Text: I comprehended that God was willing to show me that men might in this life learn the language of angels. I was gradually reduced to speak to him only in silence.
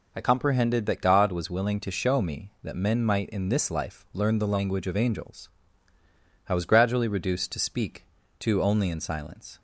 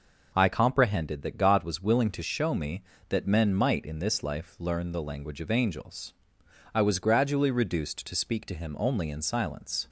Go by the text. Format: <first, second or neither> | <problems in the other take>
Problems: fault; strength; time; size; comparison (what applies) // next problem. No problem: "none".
second | skips "him"; at 8.6 s